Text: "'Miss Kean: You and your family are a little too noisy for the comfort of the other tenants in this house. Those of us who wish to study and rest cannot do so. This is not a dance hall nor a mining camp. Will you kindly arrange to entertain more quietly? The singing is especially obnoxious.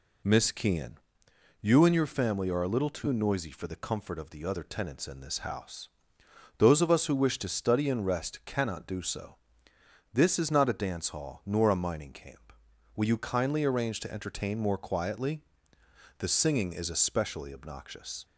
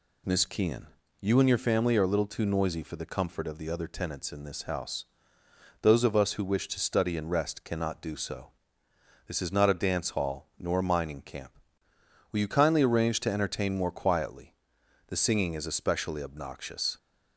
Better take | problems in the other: neither | none

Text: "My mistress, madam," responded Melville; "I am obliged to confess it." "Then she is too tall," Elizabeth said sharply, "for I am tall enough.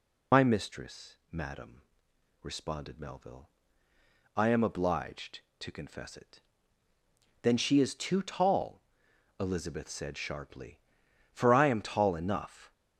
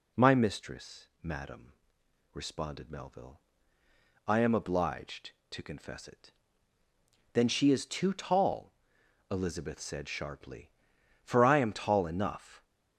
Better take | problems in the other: second | loses the start of "My"; at 0.3 s; 80 ms

